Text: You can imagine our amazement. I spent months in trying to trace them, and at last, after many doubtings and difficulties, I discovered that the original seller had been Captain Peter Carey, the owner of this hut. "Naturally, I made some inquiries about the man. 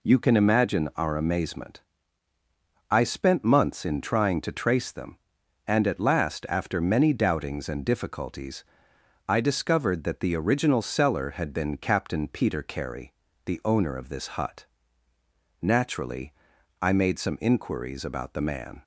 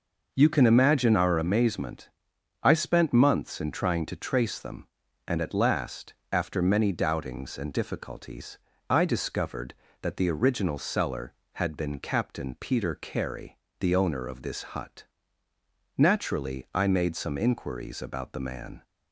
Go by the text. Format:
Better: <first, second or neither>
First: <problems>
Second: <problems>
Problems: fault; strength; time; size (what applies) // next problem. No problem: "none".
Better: neither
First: none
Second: none